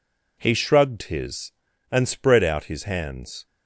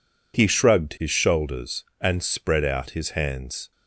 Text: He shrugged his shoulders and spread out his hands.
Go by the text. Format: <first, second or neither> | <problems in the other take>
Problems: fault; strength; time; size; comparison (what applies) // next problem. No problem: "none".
second | skips "shoulders"; at 1.7 s